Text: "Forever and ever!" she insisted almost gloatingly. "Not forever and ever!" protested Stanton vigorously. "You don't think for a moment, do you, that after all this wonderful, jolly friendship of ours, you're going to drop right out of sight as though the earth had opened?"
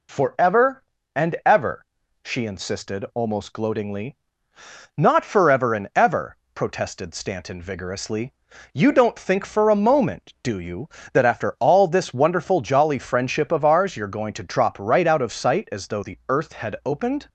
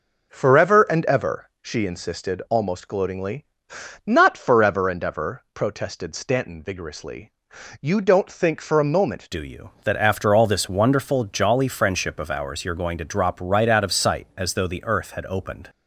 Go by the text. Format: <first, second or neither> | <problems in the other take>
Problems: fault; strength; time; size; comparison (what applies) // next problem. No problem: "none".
first | changes voice at "do"; from 9.3 s on; 6.3 s long